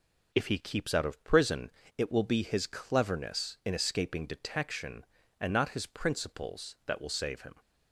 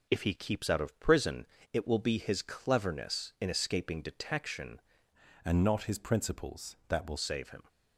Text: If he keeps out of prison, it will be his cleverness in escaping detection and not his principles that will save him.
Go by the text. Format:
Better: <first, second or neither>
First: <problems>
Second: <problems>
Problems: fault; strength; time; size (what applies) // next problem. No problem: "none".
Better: first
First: none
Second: changes voice from "and" to "will"; from 5.4 to 7.1 s; 1.7 s long